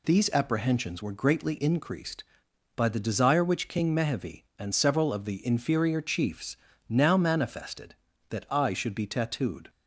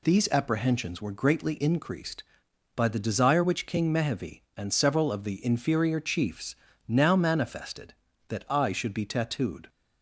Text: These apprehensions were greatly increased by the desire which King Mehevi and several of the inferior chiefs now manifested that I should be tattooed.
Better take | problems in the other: neither | pauses between "chiefs" and "now"; slight; the same in both

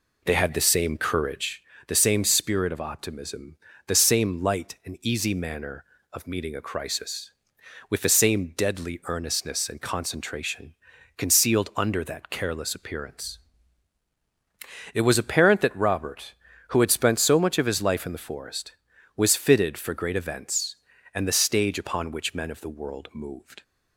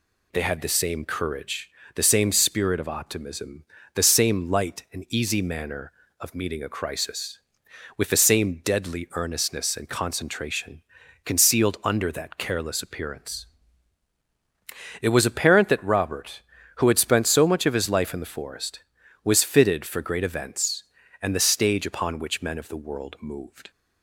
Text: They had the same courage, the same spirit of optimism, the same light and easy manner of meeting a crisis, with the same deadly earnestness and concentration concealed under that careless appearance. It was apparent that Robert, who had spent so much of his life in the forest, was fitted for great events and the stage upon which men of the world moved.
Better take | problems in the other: second | starts louder than the rest; slight; until 1.7 s; 3.5 dB // pauses between "concentration" and "concealed"; at 10.7 s; 0.42 s long; also in the second

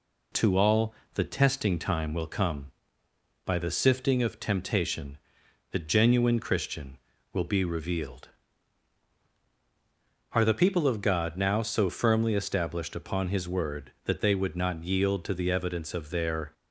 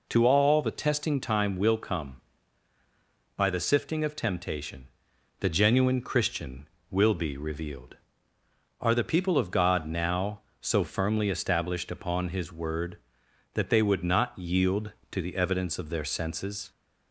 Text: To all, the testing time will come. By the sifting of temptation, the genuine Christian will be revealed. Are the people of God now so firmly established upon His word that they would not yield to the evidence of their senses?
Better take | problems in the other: second | stops before "senses"; at 16.5 s

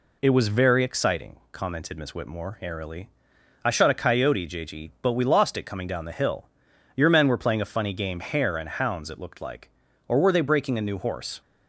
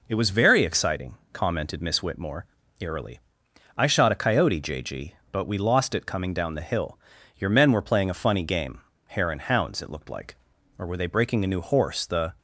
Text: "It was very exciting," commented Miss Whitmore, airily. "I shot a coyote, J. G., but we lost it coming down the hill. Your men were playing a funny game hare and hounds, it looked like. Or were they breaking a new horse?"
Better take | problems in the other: first | pauses between "game" and "hare"; slight; at 8.8 s; 0.24 s long // goes on to say "The"; slight; from 12.0 s on; 0.28 s long

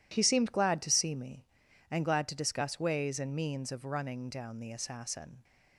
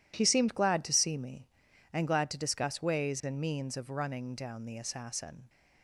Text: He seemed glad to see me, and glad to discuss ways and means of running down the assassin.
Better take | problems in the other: neither | none

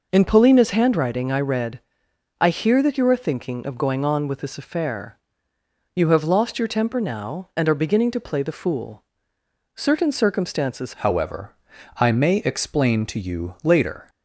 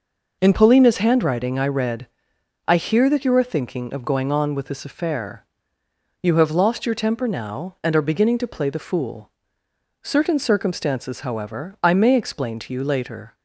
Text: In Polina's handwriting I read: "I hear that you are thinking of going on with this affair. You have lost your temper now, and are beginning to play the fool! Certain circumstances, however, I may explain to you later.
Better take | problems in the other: second | changes voice at "however"; from 10.9 s on; 3.1 s long

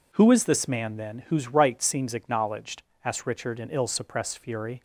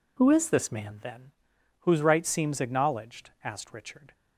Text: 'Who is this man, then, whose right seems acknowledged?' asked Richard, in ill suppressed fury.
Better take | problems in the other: first | stops before "in ill suppressed fury"; at 4.1 s

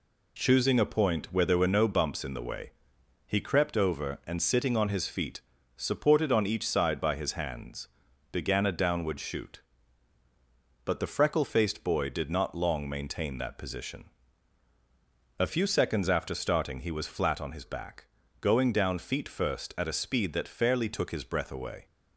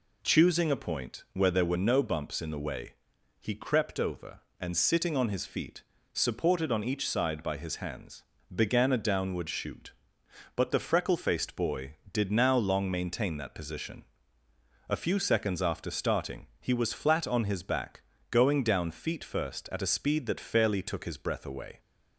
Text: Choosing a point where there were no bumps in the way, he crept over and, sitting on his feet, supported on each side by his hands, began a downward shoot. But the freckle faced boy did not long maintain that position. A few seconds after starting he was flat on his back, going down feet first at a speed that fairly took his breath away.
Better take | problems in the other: first | says "now" for "not"; at 12.3 s

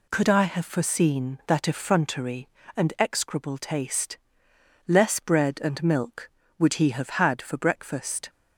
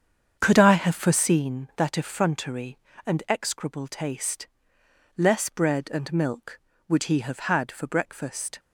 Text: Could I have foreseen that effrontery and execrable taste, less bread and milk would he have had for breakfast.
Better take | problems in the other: first | starts louder than the rest; strong; until 1.4 s; 7.5 dB

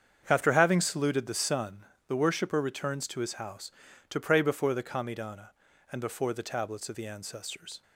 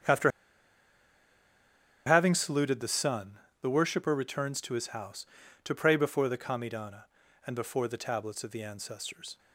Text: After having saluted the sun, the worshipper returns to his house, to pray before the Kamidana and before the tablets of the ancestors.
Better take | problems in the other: first | starts louder than the rest; strong; until 2.8 s; 7.5 dB; strong in the first // pauses between "After" and "having"; strong; at 0.3 s; 1.7 s long

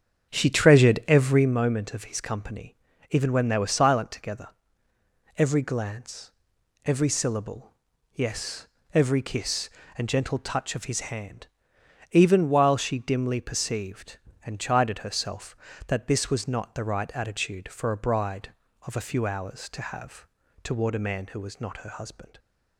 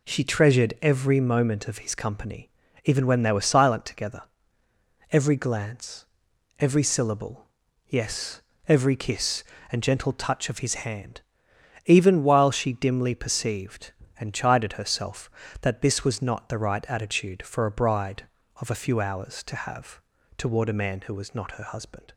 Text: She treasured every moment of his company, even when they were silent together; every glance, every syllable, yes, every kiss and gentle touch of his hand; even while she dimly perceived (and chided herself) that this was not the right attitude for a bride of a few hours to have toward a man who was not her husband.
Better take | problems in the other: second | starts louder than the rest; strong; until 1.6 s; 8 dB // pauses between "have" and "toward"; slight; at 20.2 s; 0.36 s long; slight in the second

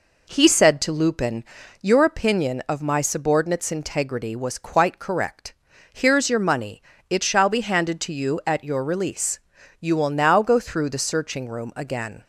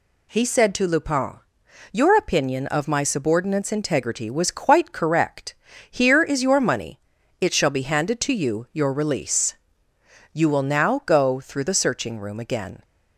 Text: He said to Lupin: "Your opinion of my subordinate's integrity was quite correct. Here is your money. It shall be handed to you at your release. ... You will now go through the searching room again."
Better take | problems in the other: first | skips "at"; at 8.7 s

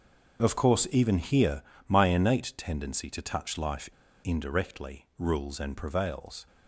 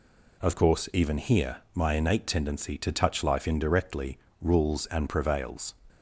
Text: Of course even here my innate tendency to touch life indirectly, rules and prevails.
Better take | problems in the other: second | starts louder than the rest; until 1.4 s; 7 dB // pauses between "here" and "my"; slight; at 1.6 s; 0.26 s long; slight in the second // pauses between "life" and "indirectly"; slight; at 3.9 s; 0.32 s long

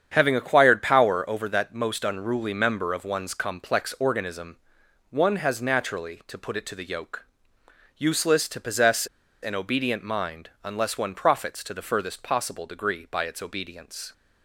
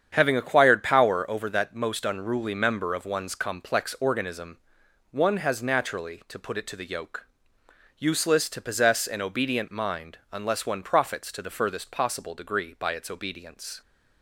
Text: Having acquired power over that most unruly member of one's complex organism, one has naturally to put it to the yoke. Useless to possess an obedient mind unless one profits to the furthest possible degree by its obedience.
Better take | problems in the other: second | starts louder than the rest; strong; until 1.1 s; 8.5 dB; strong in the second // pauses between "possess" and "an"; slight; at 9.0 s; 0.36 s long

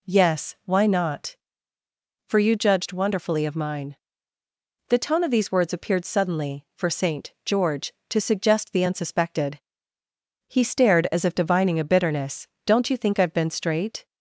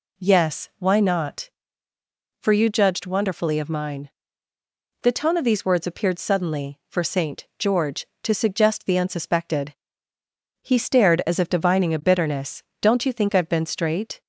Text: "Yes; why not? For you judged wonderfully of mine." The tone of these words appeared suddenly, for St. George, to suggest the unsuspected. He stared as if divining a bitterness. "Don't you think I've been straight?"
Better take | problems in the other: neither | none

